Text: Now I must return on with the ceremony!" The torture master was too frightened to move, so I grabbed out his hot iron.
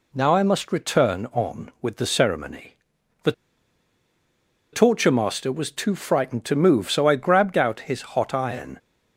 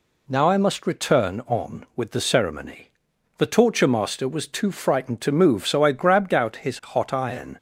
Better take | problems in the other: second | pauses between "The" and "torture"; strong; at 3.3 s; 1.4 s long

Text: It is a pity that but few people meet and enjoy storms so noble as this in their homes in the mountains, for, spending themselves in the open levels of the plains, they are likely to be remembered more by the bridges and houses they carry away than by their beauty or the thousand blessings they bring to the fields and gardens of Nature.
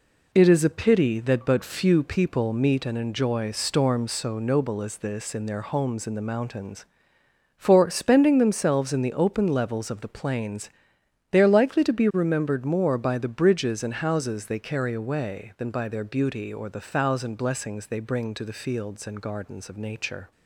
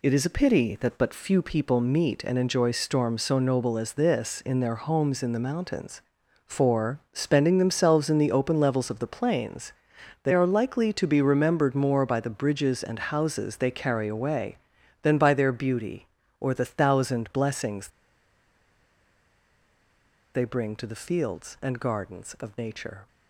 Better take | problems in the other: first | pauses between "blessings" and "they"; strong; at 17.8 s; 2.4 s long

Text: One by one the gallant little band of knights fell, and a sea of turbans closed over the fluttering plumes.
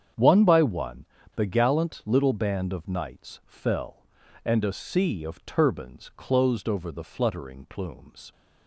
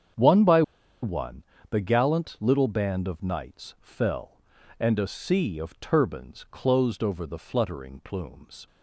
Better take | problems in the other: first | starts louder than the rest; strong; until 1.8 s; 8 dB; strong in the first // pauses between "by" and "one"; at 0.6 s; 0.40 s long // pauses between "one" and "the"; slight; at 1.4 s; 0.26 s long; slight in the first

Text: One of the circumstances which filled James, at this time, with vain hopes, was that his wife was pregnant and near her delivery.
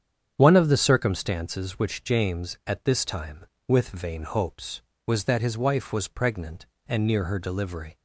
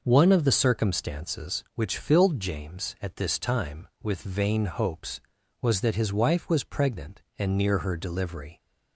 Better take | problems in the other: second | starts louder than the rest; strong; until 1.3 s; 8 dB // skips "filled"; at 2.0 s

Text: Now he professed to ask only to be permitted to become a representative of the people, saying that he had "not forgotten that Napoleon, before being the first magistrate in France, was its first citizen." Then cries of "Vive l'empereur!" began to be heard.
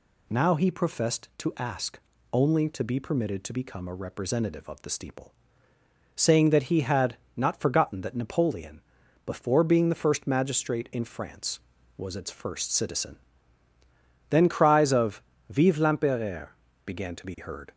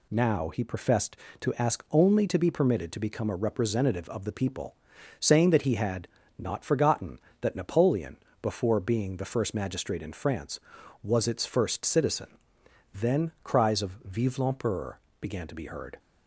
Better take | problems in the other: second | pauses between "ask" and "only"; slight; at 1.9 s; 0.34 s long // says "steeple" for "people"; at 4.8 s // pauses between "had" and "not"; slight; at 7.1 s; 0.22 s long; slight in the second // pauses between "of" and "Vive"; slight; at 15.2 s; 0.26 s long

